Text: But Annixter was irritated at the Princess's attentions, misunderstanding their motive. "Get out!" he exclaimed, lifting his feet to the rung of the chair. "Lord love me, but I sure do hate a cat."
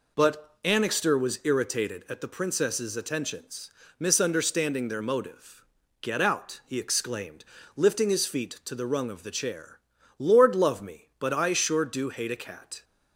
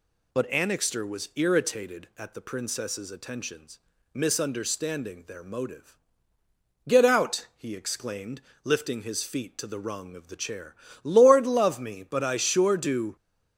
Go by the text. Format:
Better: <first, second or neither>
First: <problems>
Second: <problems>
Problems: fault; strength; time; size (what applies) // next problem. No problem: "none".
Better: first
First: none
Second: stops before "hate a cat"; at 13.1 s